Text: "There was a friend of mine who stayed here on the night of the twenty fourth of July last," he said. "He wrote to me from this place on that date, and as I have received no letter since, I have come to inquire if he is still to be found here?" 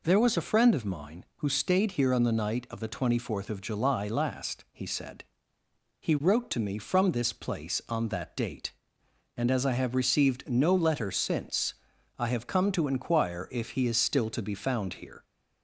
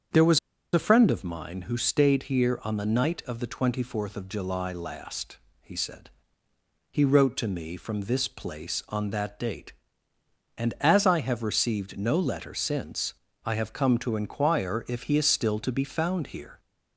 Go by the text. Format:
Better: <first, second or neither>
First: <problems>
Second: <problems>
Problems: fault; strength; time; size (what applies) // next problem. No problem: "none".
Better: first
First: none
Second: starts louder than the rest; strong; until 1.4 s; 7.5 dB // pauses between "was" and "a"; slight; at 0.3 s; 0.35 s long